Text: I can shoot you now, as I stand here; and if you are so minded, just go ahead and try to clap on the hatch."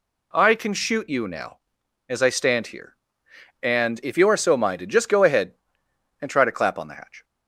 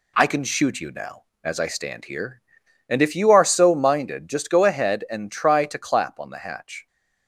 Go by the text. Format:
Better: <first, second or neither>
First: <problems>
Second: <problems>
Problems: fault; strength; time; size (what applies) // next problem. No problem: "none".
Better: neither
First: none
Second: none